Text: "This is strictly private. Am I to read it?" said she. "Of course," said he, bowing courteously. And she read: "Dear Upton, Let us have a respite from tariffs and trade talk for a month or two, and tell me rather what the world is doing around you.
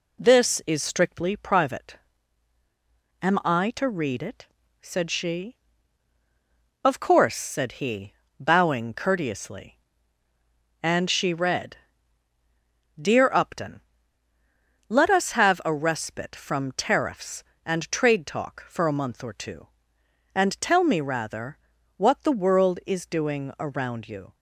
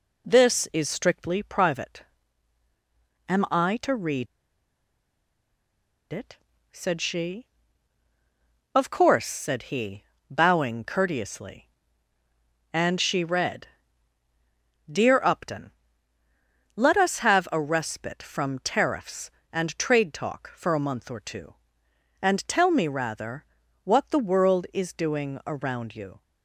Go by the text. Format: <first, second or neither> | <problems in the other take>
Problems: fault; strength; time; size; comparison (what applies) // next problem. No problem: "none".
first | pauses between "read" and "it"; strong; at 4.2 s; 1.8 s long // pauses between "rather" and "what"; at 23.4 s; 0.40 s long; also in the first